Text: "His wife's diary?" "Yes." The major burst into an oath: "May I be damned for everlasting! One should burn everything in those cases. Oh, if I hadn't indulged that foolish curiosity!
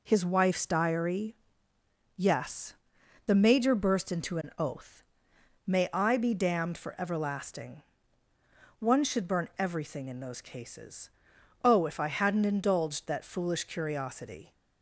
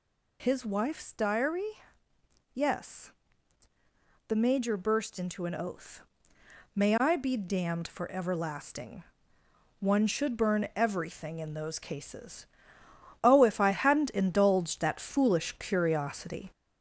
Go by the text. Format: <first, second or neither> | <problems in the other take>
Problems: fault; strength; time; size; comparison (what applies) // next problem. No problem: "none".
first | gets louder; noticeable; throughout; 4.5 dB